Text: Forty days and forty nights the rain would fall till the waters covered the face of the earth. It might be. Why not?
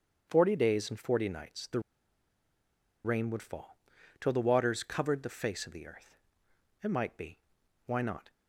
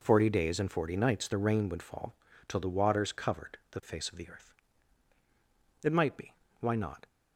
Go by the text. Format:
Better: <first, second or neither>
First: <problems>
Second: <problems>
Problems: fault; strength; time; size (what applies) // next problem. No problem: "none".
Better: second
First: starts louder than the rest; until 1.3 s; 7 dB // pauses between "the" and "rain"; strong; at 1.7 s; 1.2 s long // pauses between "fall" and "till"; at 3.7 s; 0.42 s long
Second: pauses between "fall" and "till"; slight; at 2.1 s; 0.32 s long